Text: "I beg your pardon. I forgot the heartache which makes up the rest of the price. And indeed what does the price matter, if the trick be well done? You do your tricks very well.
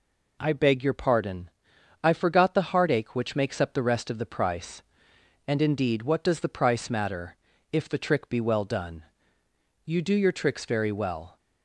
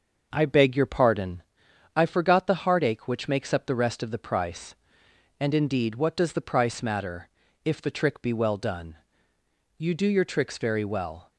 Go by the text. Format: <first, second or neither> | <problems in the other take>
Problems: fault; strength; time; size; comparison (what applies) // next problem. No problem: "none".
first | starts louder than the rest; until 1.6 s; 6 dB